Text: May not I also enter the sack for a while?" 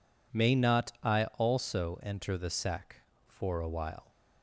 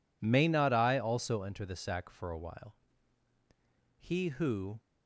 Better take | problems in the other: first | goes on to say "He who"; noticeable; from 3.9 s on; 0.82 s long

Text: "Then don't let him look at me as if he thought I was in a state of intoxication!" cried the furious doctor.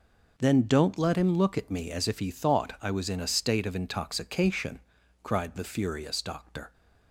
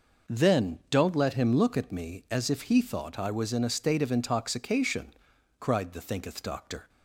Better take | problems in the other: first | says "thinketh" for "furious"; at 6.0 s

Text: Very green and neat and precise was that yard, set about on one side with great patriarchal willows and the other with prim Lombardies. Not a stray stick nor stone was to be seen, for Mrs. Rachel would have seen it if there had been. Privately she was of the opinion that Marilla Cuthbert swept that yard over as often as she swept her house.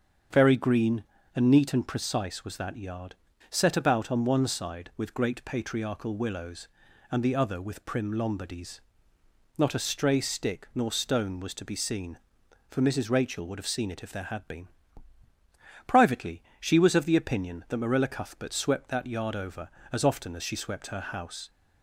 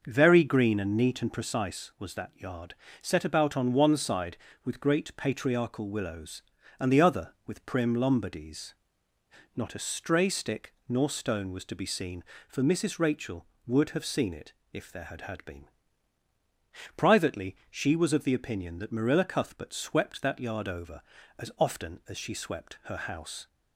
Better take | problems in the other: first | starts louder than the rest; noticeable; until 1.0 s; 6 dB; strong in the first // pauses between "stick" and "nor"; slight; at 10.7 s; 0.16 s long // pauses between "it" and "if"; slight; at 14.5 s; 0.22 s long // says "had" twice; at 15.2 s // pauses between "Privately" and "she"; slight; at 17.5 s; 0.16 s long; slight in the first

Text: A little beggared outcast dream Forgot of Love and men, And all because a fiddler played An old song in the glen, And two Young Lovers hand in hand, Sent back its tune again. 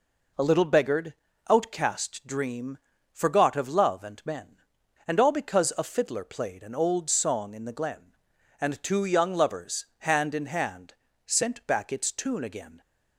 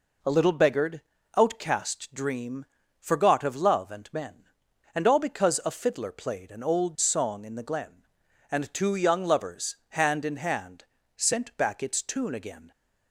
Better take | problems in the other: neither | pauses between "beggared" and "outcast"; slight; the same in both // pauses between "dream" and "Forgot"; slight; the same in both

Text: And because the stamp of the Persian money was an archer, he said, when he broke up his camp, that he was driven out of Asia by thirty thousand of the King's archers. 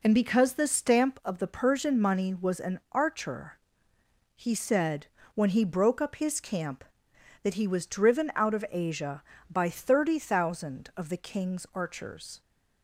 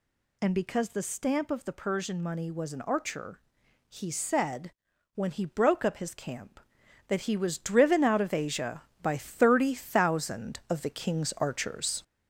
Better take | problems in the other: first | gets louder; noticeable; throughout; 4.5 dB

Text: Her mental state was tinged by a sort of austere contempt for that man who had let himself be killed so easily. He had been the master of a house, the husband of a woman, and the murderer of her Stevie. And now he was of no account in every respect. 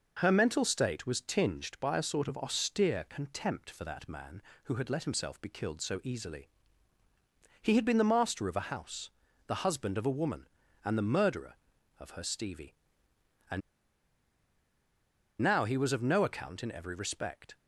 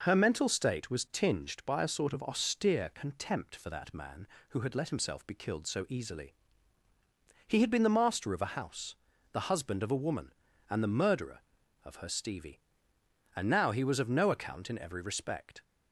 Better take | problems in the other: second | pauses between "And" and "now"; strong; at 13.6 s; 1.8 s long

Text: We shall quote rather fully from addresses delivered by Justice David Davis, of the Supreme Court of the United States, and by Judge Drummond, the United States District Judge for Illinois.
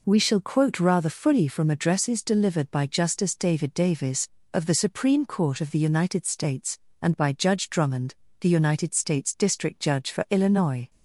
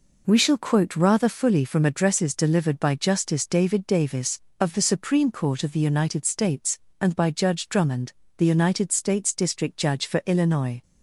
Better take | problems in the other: neither | none

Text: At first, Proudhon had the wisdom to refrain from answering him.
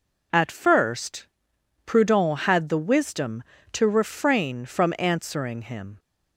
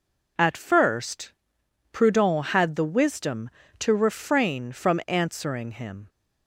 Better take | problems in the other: neither | none

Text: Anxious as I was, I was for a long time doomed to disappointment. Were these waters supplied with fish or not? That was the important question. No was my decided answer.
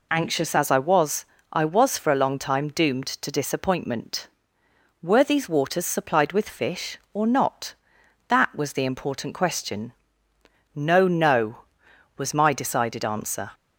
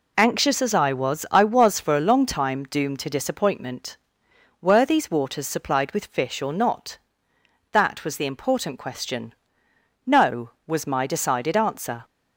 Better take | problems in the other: second | says "No" twice; at 11.0 s

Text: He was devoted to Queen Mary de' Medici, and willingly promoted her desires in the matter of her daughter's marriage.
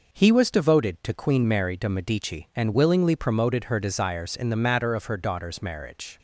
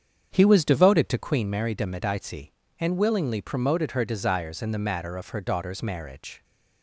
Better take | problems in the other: first | starts louder than the rest; strong; until 1.4 s; 7.5 dB

